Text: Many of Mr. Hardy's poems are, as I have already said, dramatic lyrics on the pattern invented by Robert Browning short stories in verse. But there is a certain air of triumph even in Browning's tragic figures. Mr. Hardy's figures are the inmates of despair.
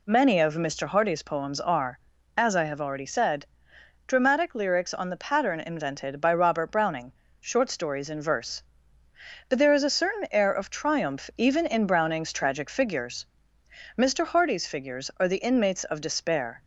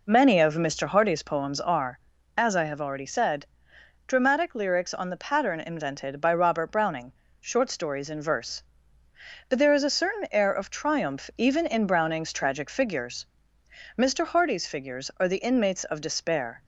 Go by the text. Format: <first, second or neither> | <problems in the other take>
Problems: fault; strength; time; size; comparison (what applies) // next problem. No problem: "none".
first | starts louder than the rest; noticeable; until 1.8 s; 4.5 dB // pauses between "Browning" and "short"; slight; at 7.1 s; 0.26 s long; slight in the first